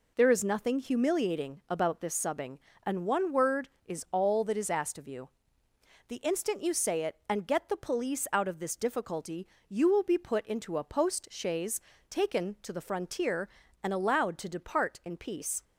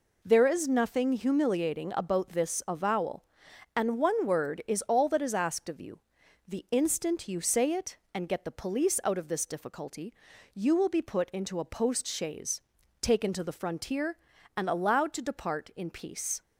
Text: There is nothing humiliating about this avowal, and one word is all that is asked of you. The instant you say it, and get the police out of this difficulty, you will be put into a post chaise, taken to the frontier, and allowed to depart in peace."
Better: second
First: says "subbing" for "avowal"; at 2.1 s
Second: none

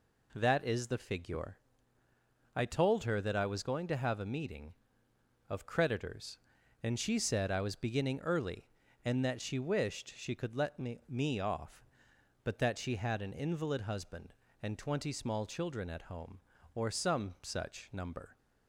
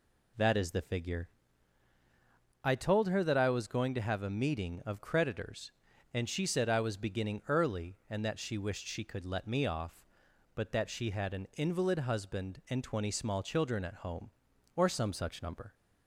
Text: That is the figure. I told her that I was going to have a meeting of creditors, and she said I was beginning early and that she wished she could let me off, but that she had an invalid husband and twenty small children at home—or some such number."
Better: second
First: says "me" twice; at 11.0 s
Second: none

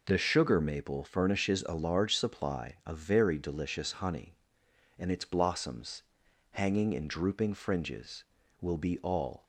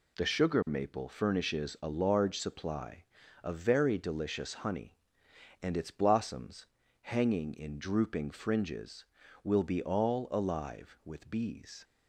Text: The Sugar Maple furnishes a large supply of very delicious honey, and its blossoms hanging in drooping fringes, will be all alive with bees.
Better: second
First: pauses between "blossoms" and "hanging"; noticeable; at 6.0 s; 0.48 s long // stops before "alive with bees"; at 9.4 s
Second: pauses between "blossoms" and "hanging"; slight; at 6.6 s; 0.36 s long

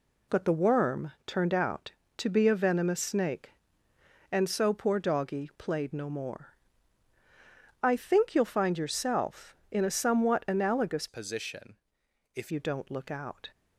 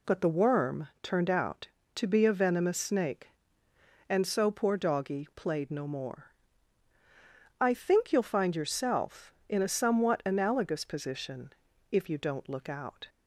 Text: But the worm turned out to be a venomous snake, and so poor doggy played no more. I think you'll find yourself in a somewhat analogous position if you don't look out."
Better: second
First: changes voice from "position" to "if"; from 11.0 to 12.5 s; 1.5 s long // pauses between "position" and "if"; noticeable; at 11.7 s; 0.58 s long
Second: pauses between "position" and "if"; at 11.5 s; 0.40 s long

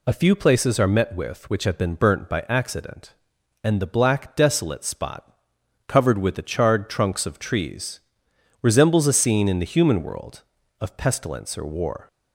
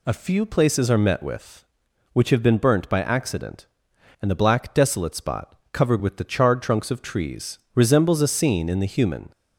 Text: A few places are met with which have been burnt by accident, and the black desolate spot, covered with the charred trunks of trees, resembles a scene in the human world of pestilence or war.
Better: first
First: none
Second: stops before "world of pestilence or war"; at 9.3 s

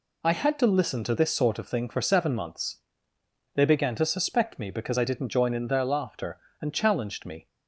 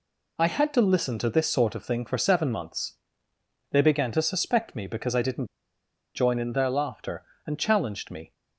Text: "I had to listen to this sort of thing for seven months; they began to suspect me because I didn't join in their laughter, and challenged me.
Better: first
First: none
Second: pauses between "didn't" and "join"; noticeable; at 5.4 s; 0.68 s long

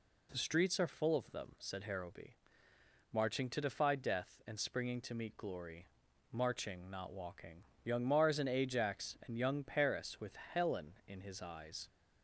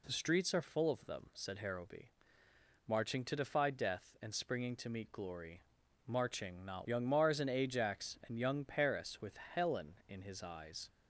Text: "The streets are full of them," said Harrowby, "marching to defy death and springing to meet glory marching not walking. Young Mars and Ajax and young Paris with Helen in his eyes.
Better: first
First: pauses between "glory" and "marching"; at 5.8 s; 0.42 s long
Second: pauses between "glory" and "marching"; at 5.6 s; 0.42 s long // skips "walking"; at 6.8 s

